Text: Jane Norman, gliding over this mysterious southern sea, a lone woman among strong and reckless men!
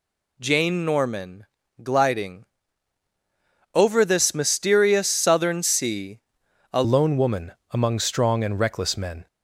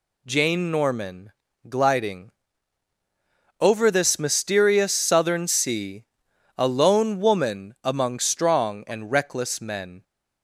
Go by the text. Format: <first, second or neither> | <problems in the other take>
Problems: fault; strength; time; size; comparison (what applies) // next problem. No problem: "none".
second | pauses between "gliding" and "over"; strong; at 2.4 s; 1.3 s long; strong in the second // changes voice at "lone"; from 6.8 s on; 2.4 s long // pauses between "woman" and "among"; slight; at 7.5 s; 0.16 s long